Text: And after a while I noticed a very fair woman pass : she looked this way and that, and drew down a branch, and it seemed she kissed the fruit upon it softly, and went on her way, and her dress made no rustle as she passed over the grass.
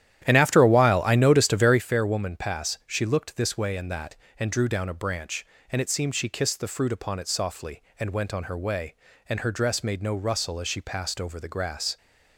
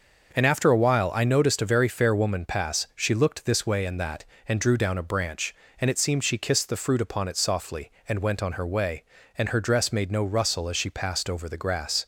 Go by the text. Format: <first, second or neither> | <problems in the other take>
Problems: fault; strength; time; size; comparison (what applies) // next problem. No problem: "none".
second | starts louder than the rest; strong; until 1.8 s; 11.5 dB